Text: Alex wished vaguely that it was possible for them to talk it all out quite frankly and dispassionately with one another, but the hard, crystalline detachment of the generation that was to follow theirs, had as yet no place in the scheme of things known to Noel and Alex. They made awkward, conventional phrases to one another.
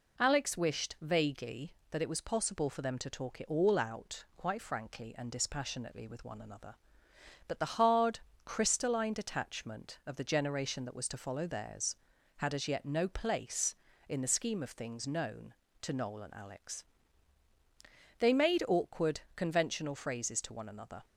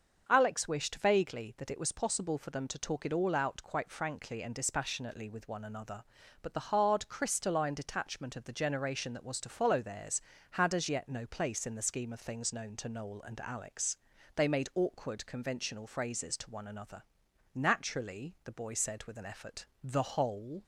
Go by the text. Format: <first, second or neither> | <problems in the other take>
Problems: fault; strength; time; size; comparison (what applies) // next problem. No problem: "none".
first | starts louder than the rest; until 1.2 s; 6.5 dB // goes on to say "Naturally the boy said with an effort the whole"; strong; from 17.5 s on; 3.1 s long